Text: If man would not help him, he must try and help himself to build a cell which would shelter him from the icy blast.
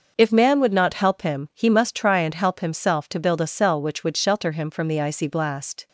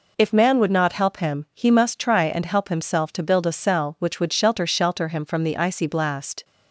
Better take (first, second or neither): first